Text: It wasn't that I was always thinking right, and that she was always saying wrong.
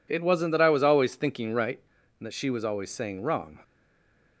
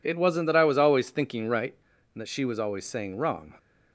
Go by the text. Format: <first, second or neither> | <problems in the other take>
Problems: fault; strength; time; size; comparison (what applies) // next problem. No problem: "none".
second | stays silent after the last word; slight; from 3.6 s on; 0.8 s long